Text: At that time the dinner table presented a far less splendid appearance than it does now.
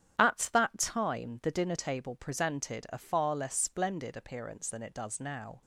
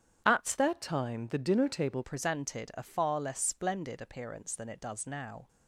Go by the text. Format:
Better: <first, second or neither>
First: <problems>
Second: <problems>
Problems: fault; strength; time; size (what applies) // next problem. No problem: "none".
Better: first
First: starts louder than the rest; strong; until 1.1 s; 10 dB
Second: starts louder than the rest; strong; until 1.2 s; 9 dB // changes voice from "that" to "table"; from 0.5 to 2.0 s; 1.5 s long